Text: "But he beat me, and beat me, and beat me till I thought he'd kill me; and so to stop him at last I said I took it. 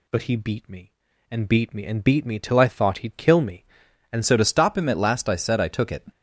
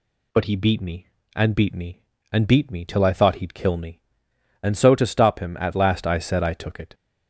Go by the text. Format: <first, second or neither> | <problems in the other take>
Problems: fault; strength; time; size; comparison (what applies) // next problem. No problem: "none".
second | changes voice at "so"; from 4.2 s on; 1.8 s long